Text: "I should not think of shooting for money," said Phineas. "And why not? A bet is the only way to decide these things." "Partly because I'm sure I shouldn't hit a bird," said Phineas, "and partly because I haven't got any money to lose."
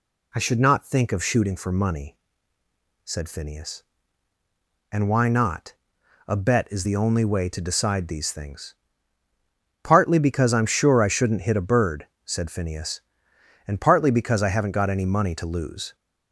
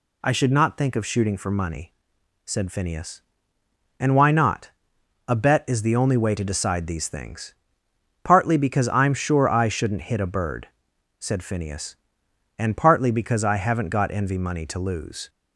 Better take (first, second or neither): first